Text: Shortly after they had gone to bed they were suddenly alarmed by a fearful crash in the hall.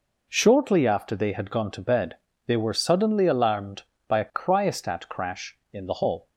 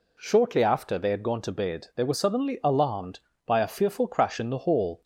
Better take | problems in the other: second | pauses between "bed" and "they"; slight; at 2.1 s; 0.32 s long // says "cryostat" for "fearful"; at 4.3 s

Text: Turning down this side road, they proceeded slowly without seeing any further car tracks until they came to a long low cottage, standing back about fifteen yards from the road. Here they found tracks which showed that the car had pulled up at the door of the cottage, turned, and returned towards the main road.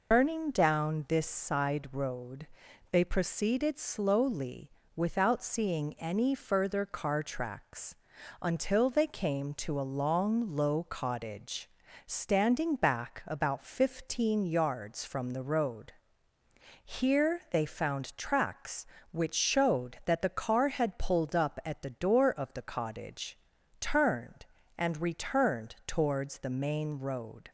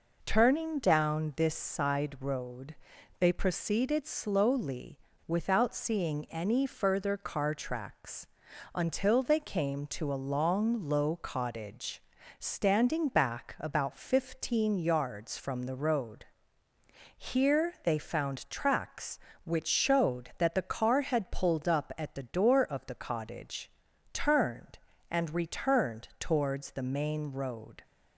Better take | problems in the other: second | loses the start of "Turning"; at 0.1 s; 185 ms // pauses between "slowly" and "without"; slight; at 4.6 s; 0.26 s long; slight in the second // pauses between "tracks" and "until"; noticeable; at 7.9 s; 0.46 s long; noticeable in the second

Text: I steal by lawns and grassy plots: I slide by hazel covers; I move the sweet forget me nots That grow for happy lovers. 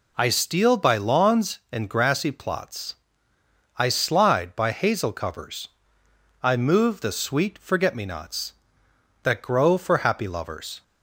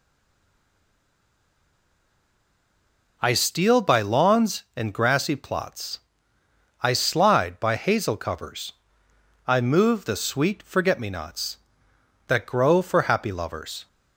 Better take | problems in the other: first | stays silent before the first word; strong; until 3.1 s; 3.1 s long

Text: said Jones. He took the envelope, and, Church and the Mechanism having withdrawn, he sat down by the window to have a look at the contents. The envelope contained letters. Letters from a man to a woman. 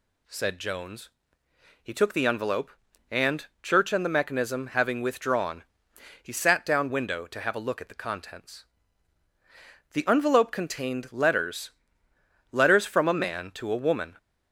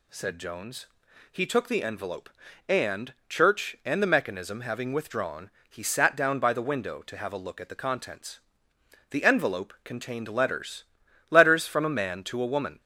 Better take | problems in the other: second | skips "by the"; at 6.8 s

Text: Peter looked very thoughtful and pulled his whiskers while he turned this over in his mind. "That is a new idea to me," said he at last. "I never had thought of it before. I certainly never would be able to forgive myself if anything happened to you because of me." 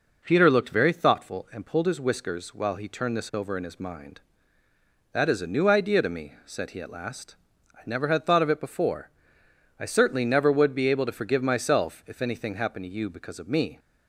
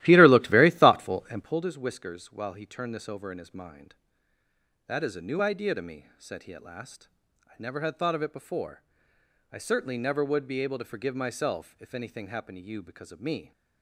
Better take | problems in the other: first | starts louder than the rest; strong; until 1.6 s; 15.5 dB

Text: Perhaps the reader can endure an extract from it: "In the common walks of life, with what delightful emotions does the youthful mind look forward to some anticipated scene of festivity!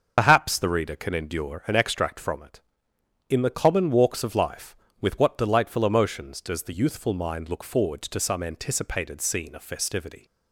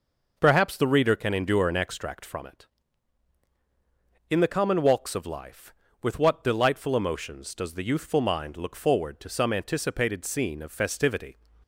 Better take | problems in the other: second | loses the start of "Perhaps"; at 0.1 s; 70 ms // starts louder than the rest; until 1.1 s; 6.5 dB

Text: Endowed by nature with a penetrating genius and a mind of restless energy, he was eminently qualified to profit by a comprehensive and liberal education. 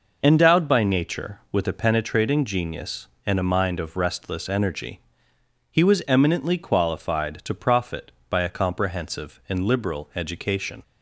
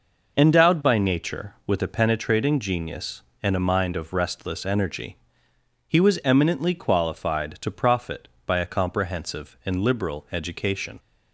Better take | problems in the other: neither | none

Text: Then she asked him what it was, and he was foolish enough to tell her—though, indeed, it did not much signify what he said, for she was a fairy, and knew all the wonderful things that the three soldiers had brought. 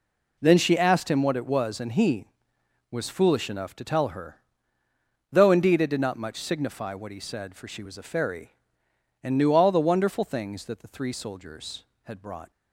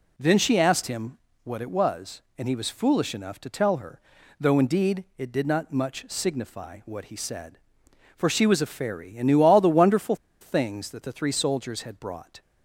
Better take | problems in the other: first | pauses between "him" and "what"; slight; at 1.1 s; 0.24 s long // pauses between "wonderful" and "things"; slight; at 10.1 s; 0.24 s long

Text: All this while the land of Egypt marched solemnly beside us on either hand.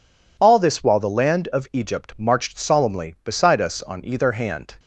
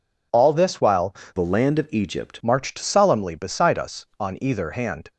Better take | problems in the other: first | changes voice from "the" to "Egypt"; from 1.3 to 2.4 s; 1.1 s long

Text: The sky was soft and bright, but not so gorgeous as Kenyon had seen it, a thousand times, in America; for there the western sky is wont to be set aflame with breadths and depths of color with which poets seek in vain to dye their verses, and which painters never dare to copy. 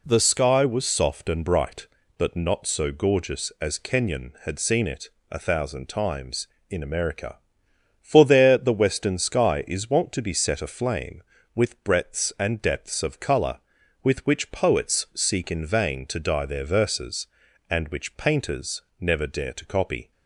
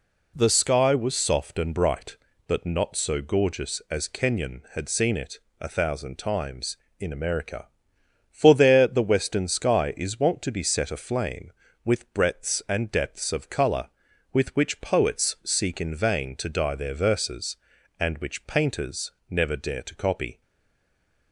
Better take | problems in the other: first | pauses between "painters" and "never"; slight; at 19.1 s; 0.18 s long; slight in the first // stays silent after the last word; from 20.4 s on; 0.9 s long

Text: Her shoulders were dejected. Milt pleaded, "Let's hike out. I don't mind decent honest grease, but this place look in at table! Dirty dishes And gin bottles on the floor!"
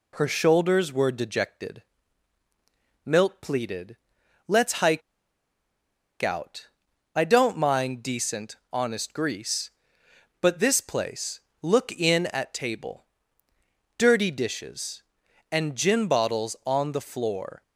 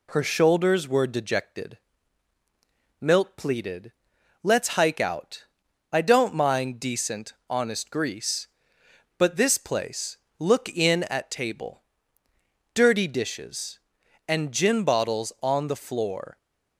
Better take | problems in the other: second | pauses between "hike" and "out"; at 5.0 s; 1.2 s long // pauses between "place" and "look"; slight; at 11.4 s; 0.22 s long; slight in the second

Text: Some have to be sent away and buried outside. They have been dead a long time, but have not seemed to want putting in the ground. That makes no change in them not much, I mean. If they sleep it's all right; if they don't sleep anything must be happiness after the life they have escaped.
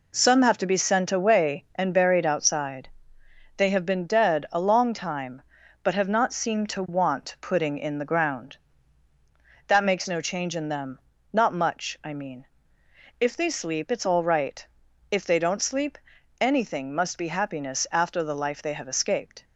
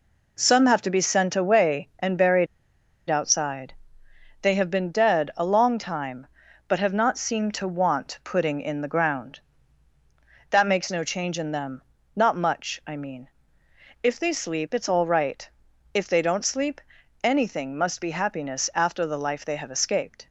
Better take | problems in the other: first | pauses between "buried" and "outside"; noticeable; at 2.4 s; 0.62 s long // pauses between "them" and "not"; slight; at 11.8 s; 0.34 s long; slight in the first // pauses between "sleep" and "anything"; at 16.8 s; 0.42 s long; also in the first

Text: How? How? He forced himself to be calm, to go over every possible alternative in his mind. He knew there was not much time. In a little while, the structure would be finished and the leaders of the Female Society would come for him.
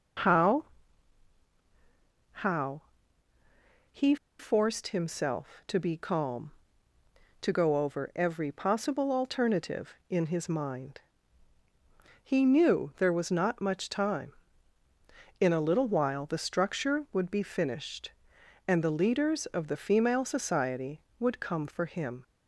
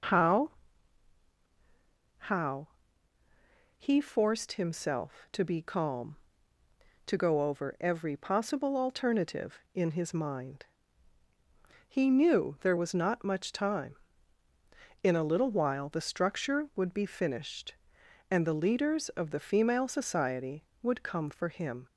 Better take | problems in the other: second | pauses between "He" and "forced"; slight; at 4.1 s; 0.23 s long

